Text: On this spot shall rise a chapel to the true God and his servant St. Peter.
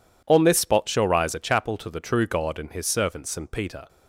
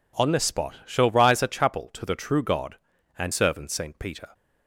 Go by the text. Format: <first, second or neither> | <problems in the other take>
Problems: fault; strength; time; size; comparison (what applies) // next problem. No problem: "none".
first | skips "his"; at 3.3 s